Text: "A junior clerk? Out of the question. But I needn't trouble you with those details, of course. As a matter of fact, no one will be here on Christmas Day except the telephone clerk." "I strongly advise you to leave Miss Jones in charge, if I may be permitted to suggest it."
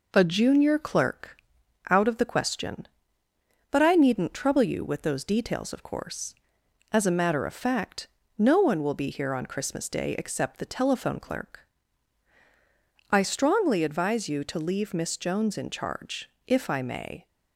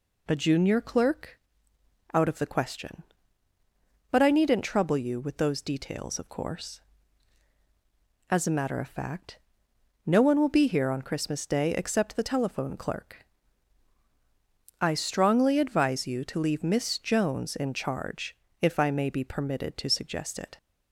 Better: second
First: stops before "be permitted to suggest it"; at 17.2 s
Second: none

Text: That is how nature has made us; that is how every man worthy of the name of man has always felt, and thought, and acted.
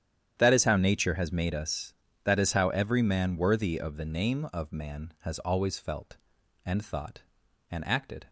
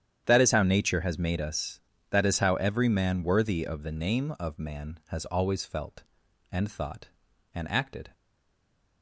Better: first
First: starts louder than the rest; strong; until 1.3 s; 9.5 dB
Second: starts louder than the rest; strong; until 1.2 s; 9.5 dB // stays silent after the last word; slight; from 8.1 s on; 0.9 s long

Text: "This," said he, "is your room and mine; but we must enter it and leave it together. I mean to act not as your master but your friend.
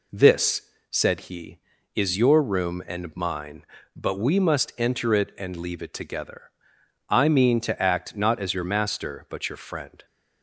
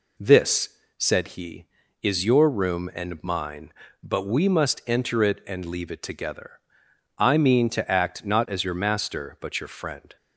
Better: neither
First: none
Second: none

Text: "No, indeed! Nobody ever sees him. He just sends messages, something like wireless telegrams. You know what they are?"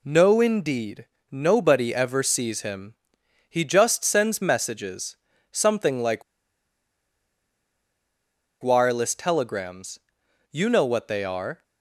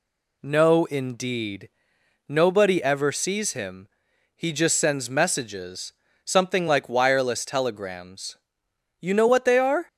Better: second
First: pauses between "like" and "wireless"; strong; at 6.2 s; 2.3 s long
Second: none

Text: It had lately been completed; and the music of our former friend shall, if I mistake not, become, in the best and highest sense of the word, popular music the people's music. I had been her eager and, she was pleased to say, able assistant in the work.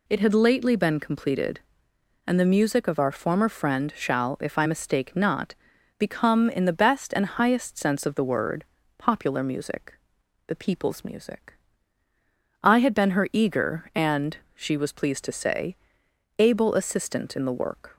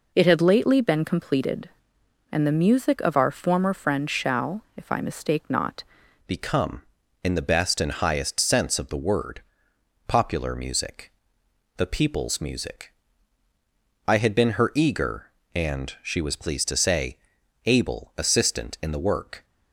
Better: first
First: pauses between "music" and "the"; noticeable; at 9.9 s; 0.52 s long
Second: changes voice at "become"; from 6.2 s on; 13.2 s long // pauses between "music" and "the"; noticeable; at 11.1 s; 0.66 s long

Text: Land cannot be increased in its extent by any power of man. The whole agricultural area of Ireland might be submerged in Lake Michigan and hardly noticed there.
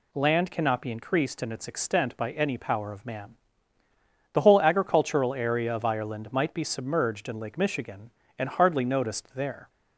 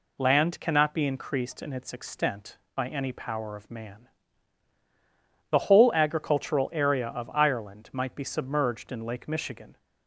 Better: first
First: none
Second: stops before "and hardly noticed there"; at 9.7 s

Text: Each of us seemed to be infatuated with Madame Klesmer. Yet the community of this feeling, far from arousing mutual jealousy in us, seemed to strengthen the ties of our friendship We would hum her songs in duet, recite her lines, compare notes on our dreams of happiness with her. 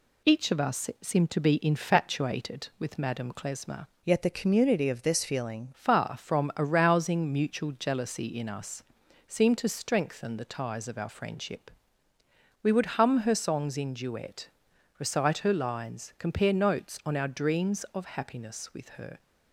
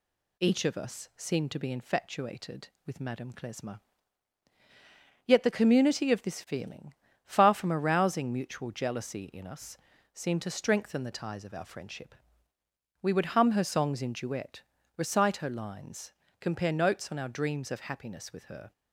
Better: second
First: changes voice from "Yet" to "feeling"; from 4.0 to 5.7 s; 1.7 s long // pauses between "friendship" and "We"; noticeable; at 11.6 s; 0.92 s long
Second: pauses between "friendship" and "We"; noticeable; at 12.1 s; 0.88 s long

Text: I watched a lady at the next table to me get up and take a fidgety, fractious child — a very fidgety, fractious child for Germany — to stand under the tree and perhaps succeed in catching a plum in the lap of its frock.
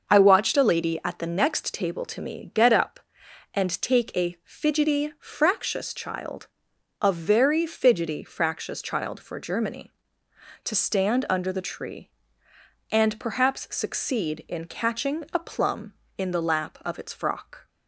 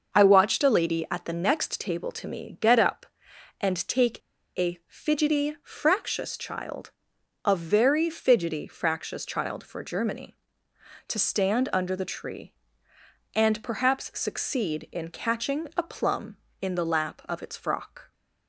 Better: first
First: starts louder than the rest; until 1.1 s; 6 dB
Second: starts louder than the rest; until 1.2 s; 6 dB // pauses between "take" and "a"; at 4.2 s; 0.38 s long

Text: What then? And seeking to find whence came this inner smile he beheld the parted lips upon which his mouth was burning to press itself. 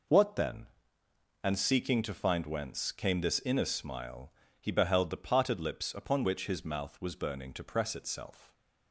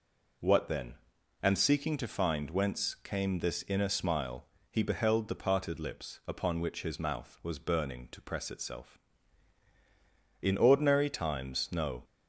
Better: first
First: pauses between "smile" and "he"; slight; at 4.3 s; 0.26 s long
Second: pauses between "smile" and "he"; slight; at 4.4 s; 0.26 s long // goes on to say "IN ordinary times no"; from 10.4 s on; 1.6 s long

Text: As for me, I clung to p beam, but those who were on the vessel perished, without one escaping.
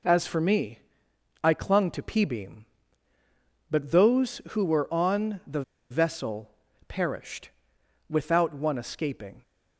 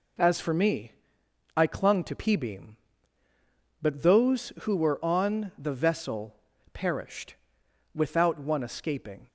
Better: second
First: pauses between "the" and "vessel"; slight; at 5.6 s; 0.28 s long // pauses between "vessel" and "perished"; at 6.4 s; 0.38 s long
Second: pauses between "vessel" and "perished"; at 6.3 s; 0.38 s long

